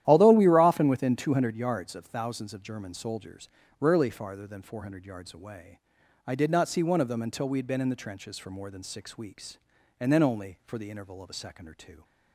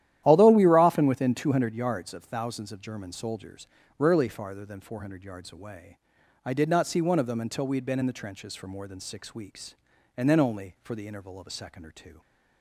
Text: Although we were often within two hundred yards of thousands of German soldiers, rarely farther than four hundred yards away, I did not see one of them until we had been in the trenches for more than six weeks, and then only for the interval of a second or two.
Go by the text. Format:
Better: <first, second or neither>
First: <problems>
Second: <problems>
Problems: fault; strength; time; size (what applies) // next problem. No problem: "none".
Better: neither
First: starts louder than the rest; strong; until 1.0 s; 12 dB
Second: starts louder than the rest; strong; until 1.2 s; 12 dB